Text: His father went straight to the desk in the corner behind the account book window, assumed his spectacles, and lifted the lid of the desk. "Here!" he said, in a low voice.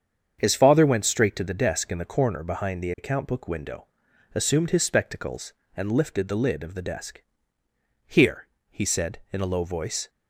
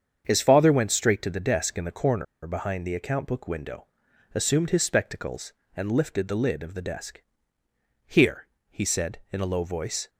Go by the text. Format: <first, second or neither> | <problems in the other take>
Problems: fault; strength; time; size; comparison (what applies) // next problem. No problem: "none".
first | starts louder than the rest; strong; until 1.2 s; 7.5 dB; strong in the first // pauses between "corner" and "behind"; slight; at 2.2 s; 0.20 s long